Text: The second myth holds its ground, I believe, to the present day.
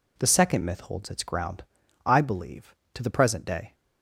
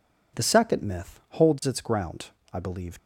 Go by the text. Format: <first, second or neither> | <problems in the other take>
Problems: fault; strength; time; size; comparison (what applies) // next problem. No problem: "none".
first | stops before "to the present day"; at 2.9 s